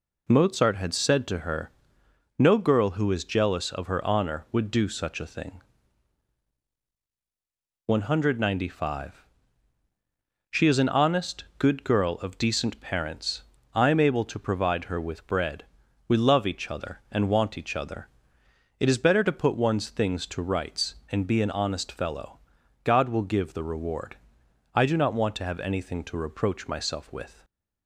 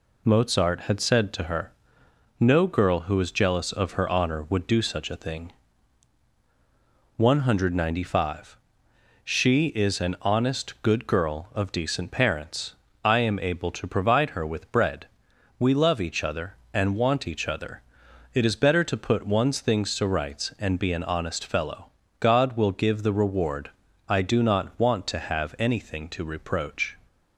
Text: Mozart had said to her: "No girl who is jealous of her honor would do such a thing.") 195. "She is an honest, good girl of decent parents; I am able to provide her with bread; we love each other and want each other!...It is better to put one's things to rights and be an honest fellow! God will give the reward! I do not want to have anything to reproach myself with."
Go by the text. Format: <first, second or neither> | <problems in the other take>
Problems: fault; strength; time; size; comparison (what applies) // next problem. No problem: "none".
first | stops before "myself with"; at 27.0 s